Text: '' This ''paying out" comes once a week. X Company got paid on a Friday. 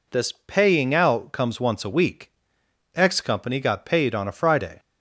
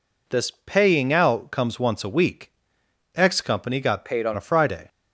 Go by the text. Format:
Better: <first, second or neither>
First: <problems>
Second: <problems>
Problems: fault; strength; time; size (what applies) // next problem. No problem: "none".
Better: first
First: none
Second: changes voice from "paid" to "on"; from 4.0 to 4.3 s; 0.3 s long